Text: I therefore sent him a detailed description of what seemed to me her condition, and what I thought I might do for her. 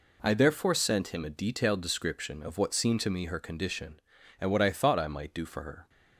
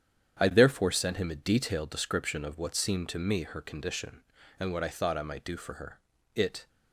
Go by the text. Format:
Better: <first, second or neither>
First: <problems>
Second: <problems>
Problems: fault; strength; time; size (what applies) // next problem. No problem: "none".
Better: first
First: none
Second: starts louder than the rest; strong; until 1.4 s; 9 dB // goes on to say "It"; slight; from 6.3 s on; 0.34 s long